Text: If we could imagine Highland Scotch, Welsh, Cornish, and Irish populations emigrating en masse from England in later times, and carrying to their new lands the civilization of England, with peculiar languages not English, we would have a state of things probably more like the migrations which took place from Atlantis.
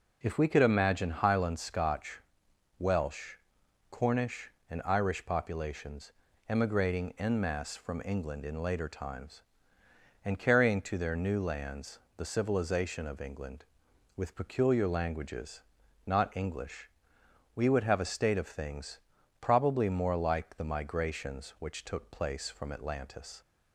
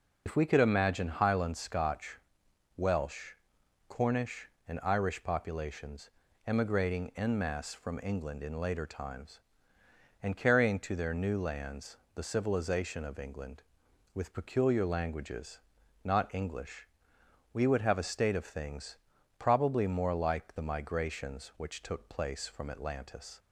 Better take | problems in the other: first | loses the start of "If"; at 0.2 s; 50 ms // pauses between "populations" and "emigrating"; slight; at 6.0 s; 0.36 s long; slight in the first // pauses between "lands" and "the"; slight; at 11.9 s; 0.20 s long; slight in the first // pauses between "languages" and "not"; at 15.5 s; 0.44 s long; also in the first // pauses between "things" and "probably"; at 18.9 s; 0.40 s long; also in the first

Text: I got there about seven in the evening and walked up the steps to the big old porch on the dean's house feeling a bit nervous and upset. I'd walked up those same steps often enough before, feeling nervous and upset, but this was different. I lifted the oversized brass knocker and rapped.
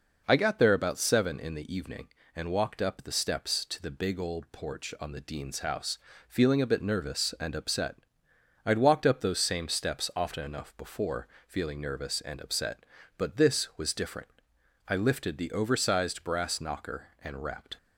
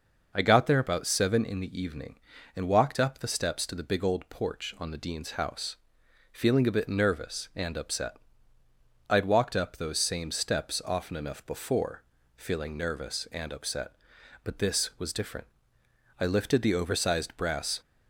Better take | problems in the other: first | pauses between "house" and "feeling"; noticeable; at 5.7 s; 0.56 s long; slight in the first // stops before "knocker and rapped"; at 17.8 s

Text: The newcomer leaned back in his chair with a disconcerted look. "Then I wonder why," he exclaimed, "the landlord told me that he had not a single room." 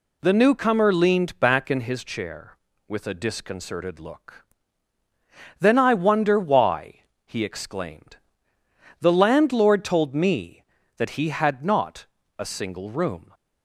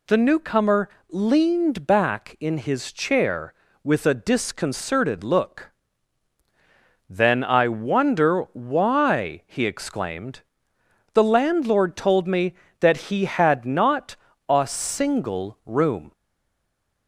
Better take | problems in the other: first | pauses between "newcomer" and "leaned"; slight; at 0.8 s; 0.22 s long // pauses between "not" and "a"; slight; at 14.1 s; 0.34 s long; slight in the first // stays silent after the last word; from 16.1 s on; 0.9 s long

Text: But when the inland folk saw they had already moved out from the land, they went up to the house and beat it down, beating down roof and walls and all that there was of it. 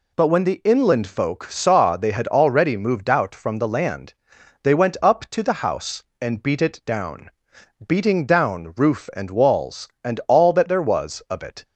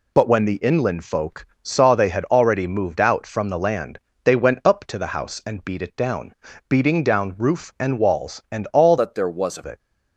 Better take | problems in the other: first | pauses between "folk" and "saw"; slight; at 1.4 s; 0.16 s long // changes voice from "that" to "of"; from 8.9 to 9.6 s; 0.7 s long

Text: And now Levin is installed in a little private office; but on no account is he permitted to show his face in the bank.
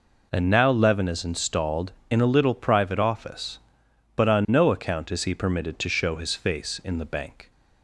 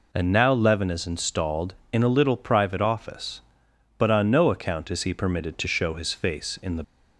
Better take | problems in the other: first | stops before "bank"; at 6.8 s

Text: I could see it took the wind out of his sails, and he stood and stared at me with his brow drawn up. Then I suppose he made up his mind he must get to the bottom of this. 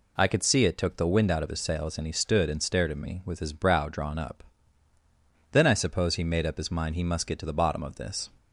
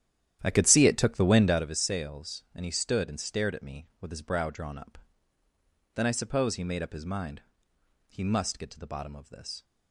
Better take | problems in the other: first | starts louder than the rest; strong; until 1.7 s; 11 dB // pauses between "mind" and "he"; noticeable; at 7.4 s; 0.68 s long

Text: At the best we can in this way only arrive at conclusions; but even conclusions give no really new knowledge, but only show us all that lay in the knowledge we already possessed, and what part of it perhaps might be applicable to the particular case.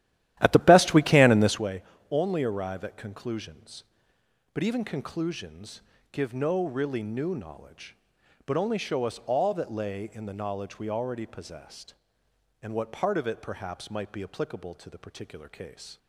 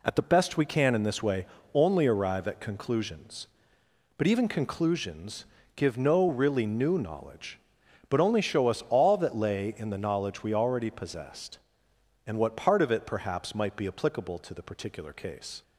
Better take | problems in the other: second | starts louder than the rest; strong; until 1.7 s; 13.5 dB // pauses between "way" and "only"; slight; at 1.8 s; 0.30 s long; slight in the second // pauses between "conclusions" and "give"; slight; at 5.8 s; 0.30 s long; slight in the second

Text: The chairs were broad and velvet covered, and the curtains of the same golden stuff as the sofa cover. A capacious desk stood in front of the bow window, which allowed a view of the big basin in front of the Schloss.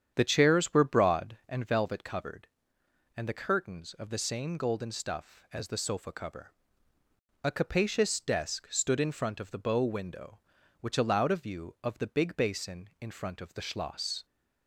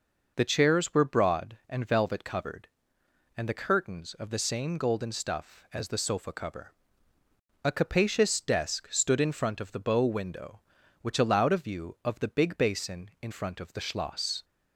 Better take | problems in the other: second | starts louder than the rest; strong; until 1.6 s; 8.5 dB

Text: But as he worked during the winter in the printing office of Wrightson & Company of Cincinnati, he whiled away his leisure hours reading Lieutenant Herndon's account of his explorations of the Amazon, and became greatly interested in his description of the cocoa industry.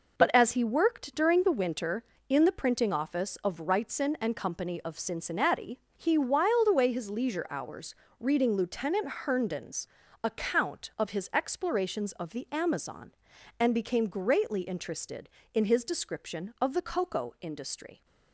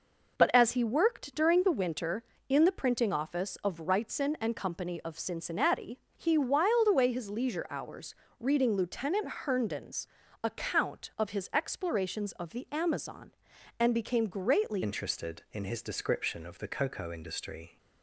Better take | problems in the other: first | pauses between "hours" and "reading"; slight; at 8.1 s; 0.24 s long; slight in the first // pauses between "Lieutenant" and "Herndon's"; slight; at 9.2 s; 0.16 s long; slight in the first // pauses between "Herndon's" and "account"; slight; at 10.0 s; 0.36 s long; slight in the first // changes voice at "interested"; from 14.8 s on; 2.9 s long

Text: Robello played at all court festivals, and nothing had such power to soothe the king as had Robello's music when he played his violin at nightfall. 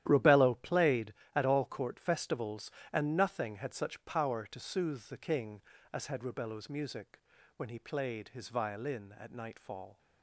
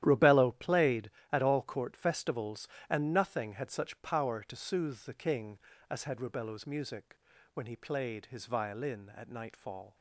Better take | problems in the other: neither | starts louder than the rest; strong; the same in both // pauses between "music" and "when"; slight; the same in both

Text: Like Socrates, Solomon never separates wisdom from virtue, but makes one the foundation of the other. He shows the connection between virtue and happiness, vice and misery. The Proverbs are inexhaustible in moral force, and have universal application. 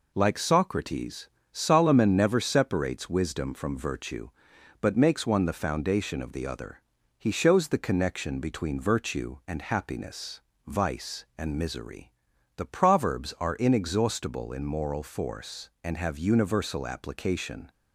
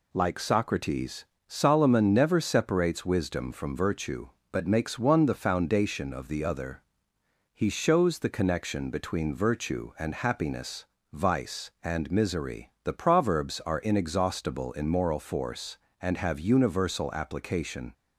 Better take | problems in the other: neither | none

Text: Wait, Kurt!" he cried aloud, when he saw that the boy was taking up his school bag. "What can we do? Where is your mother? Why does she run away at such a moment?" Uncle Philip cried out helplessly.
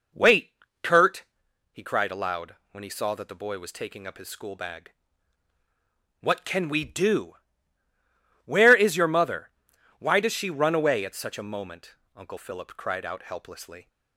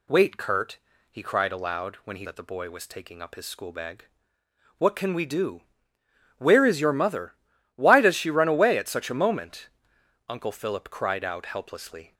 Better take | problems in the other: first | skips "saw"; at 2.2 s

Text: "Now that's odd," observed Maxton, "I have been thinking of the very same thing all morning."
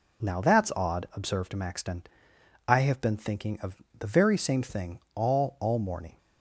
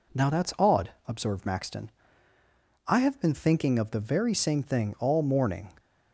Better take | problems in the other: second | pauses between "of" and "the"; slight; at 3.8 s; 0.16 s long // pauses between "thing" and "all"; slight; at 4.9 s; 0.16 s long // says "all" twice; at 5.5 s

